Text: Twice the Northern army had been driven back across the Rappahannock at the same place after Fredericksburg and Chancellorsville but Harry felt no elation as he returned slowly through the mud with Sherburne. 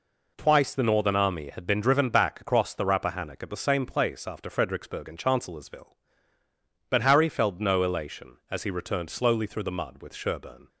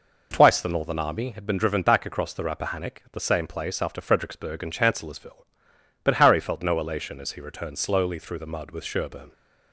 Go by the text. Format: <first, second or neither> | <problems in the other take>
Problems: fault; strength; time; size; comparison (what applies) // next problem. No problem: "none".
neither | none